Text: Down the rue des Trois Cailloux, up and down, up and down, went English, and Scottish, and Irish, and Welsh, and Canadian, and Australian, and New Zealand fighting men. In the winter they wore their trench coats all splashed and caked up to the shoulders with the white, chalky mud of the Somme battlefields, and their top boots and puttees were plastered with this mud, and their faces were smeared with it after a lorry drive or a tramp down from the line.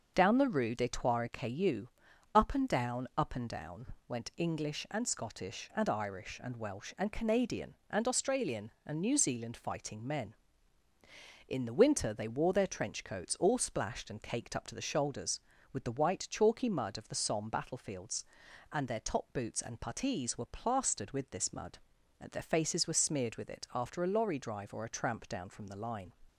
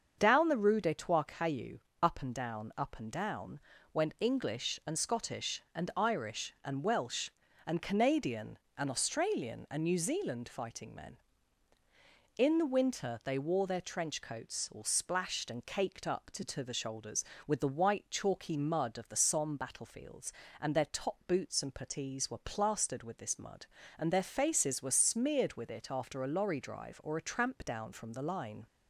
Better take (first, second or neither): first